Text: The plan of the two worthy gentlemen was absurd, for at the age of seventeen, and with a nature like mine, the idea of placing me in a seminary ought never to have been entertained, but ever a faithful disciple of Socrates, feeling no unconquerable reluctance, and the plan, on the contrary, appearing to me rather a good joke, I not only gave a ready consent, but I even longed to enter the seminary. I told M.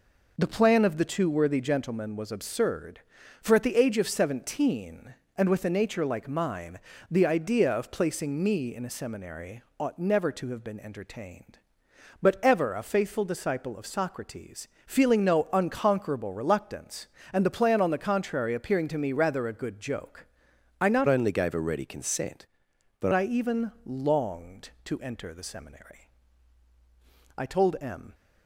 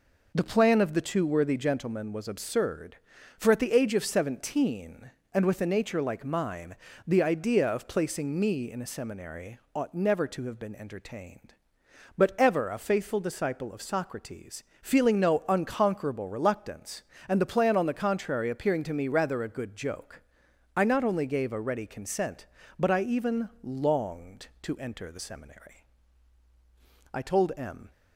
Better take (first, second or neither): second